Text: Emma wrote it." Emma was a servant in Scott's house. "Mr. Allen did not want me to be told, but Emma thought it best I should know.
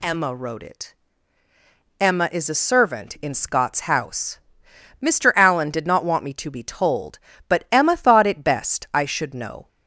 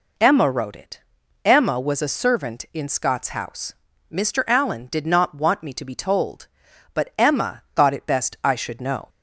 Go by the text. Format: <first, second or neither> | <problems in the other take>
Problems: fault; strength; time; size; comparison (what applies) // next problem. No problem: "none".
second | says "is" for "was"; at 2.3 s